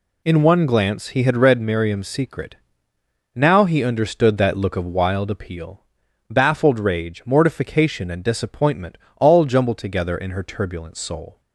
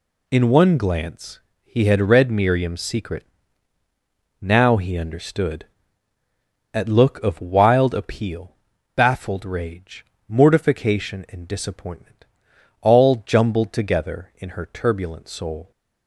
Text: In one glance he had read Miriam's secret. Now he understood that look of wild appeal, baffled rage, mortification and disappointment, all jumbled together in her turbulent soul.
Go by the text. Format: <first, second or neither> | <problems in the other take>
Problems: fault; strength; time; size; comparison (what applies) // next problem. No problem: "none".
first | pauses between "glance" and "he"; slight; at 1.3 s; 0.24 s long // says "at" for "that"; at 6.7 s